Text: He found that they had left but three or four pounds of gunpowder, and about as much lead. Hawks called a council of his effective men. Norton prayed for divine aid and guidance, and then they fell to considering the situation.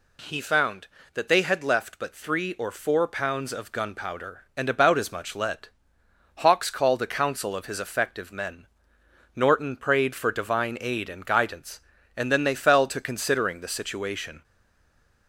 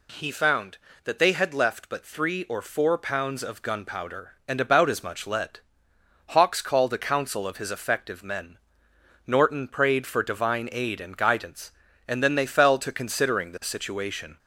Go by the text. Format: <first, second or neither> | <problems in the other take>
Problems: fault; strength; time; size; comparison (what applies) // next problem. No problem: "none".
second | stays silent after the last word; slight; from 14.4 s on; 0.8 s long